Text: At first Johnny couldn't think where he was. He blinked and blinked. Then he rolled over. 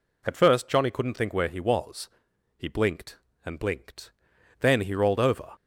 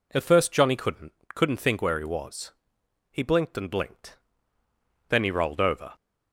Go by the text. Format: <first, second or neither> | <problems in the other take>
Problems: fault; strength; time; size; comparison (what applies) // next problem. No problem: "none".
first | says "couldn't" twice; at 1.3 s